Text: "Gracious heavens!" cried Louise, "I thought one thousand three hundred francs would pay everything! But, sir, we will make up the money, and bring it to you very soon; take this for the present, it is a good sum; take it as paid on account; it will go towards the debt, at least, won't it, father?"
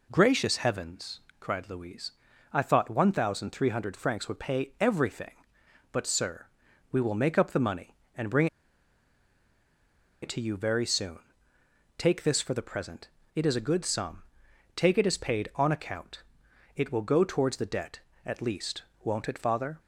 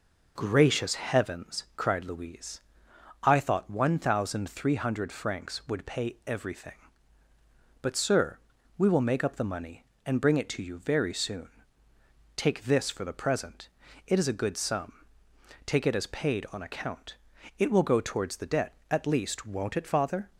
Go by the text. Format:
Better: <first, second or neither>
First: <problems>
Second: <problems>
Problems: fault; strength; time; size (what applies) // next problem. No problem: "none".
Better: second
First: pauses between "bring" and "it"; strong; at 8.4 s; 1.7 s long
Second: none